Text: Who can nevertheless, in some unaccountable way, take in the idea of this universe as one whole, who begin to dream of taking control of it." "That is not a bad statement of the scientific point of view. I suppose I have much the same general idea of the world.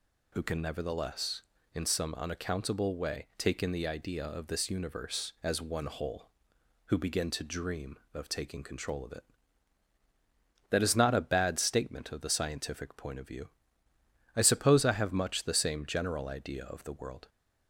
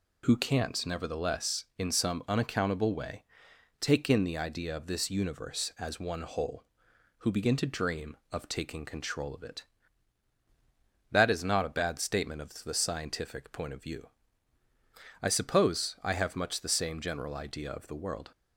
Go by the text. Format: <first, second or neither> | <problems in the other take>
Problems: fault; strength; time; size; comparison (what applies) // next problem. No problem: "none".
first | says "can't" for "can"; at 0.3 s